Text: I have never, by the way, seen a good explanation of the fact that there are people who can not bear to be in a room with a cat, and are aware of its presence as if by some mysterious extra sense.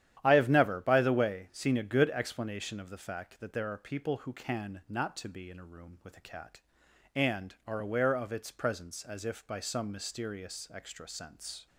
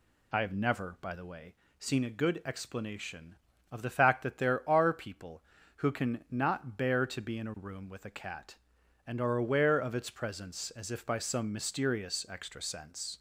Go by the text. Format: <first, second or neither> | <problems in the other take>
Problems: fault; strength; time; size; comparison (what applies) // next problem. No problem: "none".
second | starts louder than the rest; strong; until 1.2 s; 11 dB // skips "bear"; at 5.1 s